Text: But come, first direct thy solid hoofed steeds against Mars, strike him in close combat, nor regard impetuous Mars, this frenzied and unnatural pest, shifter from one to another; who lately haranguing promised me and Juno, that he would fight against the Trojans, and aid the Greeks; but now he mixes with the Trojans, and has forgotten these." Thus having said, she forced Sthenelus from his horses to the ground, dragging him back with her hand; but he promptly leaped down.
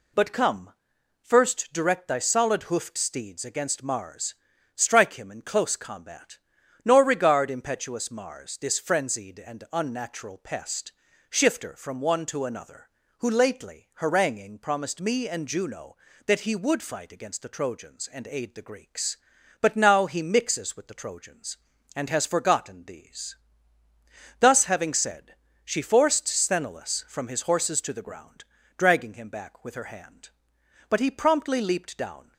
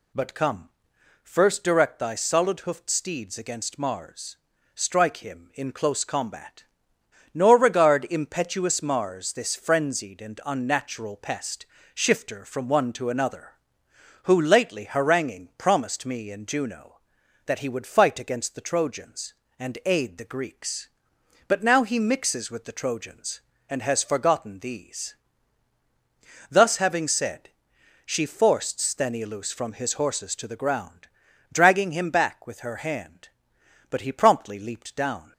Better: neither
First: none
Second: none

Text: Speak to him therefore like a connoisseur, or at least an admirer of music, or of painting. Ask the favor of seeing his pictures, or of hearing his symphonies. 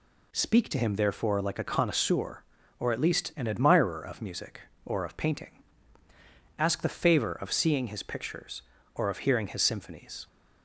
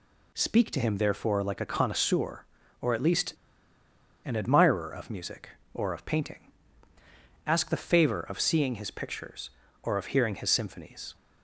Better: first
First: none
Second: pauses between "least" and "an"; noticeable; at 3.3 s; 0.89 s long

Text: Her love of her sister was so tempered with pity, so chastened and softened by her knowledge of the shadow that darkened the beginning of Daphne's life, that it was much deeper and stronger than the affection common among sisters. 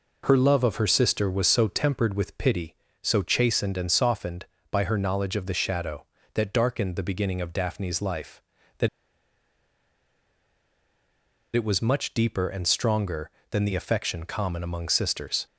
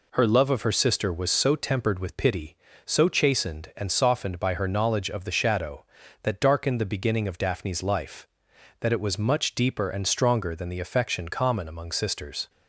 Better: second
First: pauses between "that" and "it"; strong; at 8.8 s; 2.6 s long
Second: none

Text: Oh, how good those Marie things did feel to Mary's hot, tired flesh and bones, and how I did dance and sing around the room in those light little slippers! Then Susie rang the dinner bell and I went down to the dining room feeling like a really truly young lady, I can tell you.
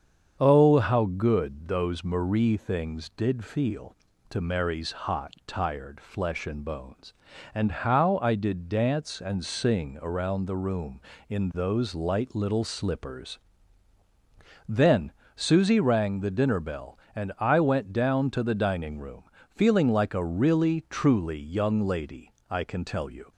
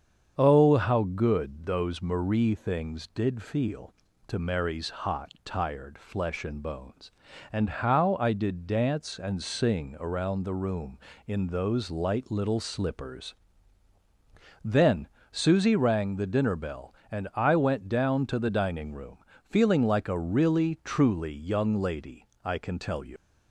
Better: first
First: starts louder than the rest; strong; until 1.4 s; 7.5 dB // pauses between "Then" and "Susie"; slight; at 15.1 s; 0.24 s long // pauses between "room" and "feeling"; slight; at 19.2 s; 0.26 s long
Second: starts louder than the rest; strong; until 1.3 s; 7.5 dB // pauses between "Then" and "Susie"; slight; at 15.0 s; 0.24 s long // pauses between "room" and "feeling"; slight; at 19.1 s; 0.26 s long // leaves "you" unfinished; at 23.1 s; 95 ms

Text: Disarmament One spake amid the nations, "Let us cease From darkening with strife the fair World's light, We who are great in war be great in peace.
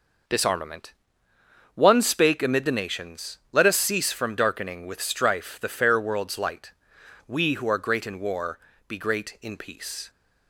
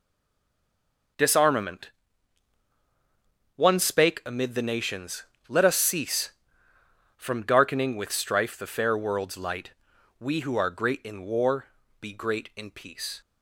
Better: first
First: pauses between "Disarmament" and "One"; noticeable; at 0.9 s; 0.82 s long // pauses between "war" and "be"; slight; at 8.5 s; 0.30 s long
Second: stays silent before the first word; noticeable; until 1.1 s; 1.1 s long // pauses between "Disarmament" and "One"; strong; at 1.9 s; 1.6 s long // pauses between "war" and "be"; slight; at 11.6 s; 0.34 s long

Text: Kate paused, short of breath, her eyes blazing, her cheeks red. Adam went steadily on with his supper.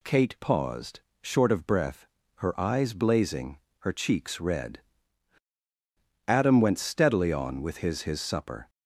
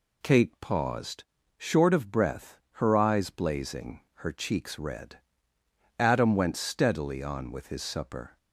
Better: second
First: says "his" twice; at 8.0 s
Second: none

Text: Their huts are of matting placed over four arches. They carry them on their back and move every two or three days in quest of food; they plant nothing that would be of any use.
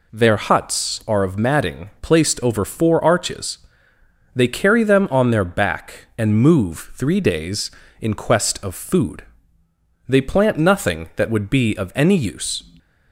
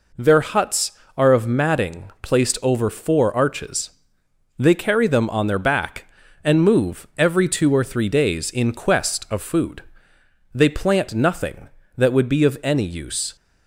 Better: second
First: skips "every two or"; at 6.9 s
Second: none

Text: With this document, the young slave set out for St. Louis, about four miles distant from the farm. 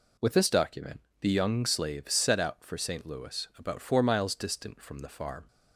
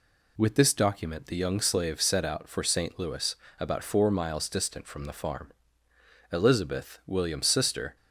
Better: first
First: none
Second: goes on to say "Elizabeth William's sister"; from 6.3 s on; 1.6 s long

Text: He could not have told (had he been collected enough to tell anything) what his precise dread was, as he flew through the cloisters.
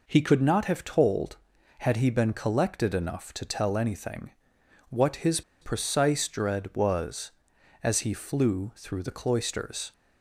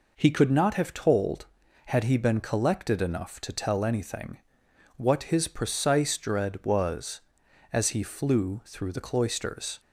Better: second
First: pauses between "his" and "precise"; slight; at 5.4 s; 0.20 s long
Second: none

